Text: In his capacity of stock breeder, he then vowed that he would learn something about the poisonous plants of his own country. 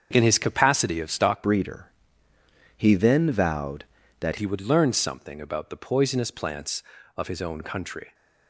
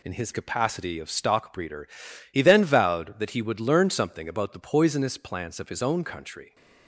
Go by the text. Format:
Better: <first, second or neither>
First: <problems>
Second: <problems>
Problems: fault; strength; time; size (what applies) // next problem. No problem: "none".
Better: second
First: starts louder than the rest; strong; until 1.1 s; 7 dB // changes voice from "breeder" to "that"; from 1.4 to 4.3 s; 2.9 s long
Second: none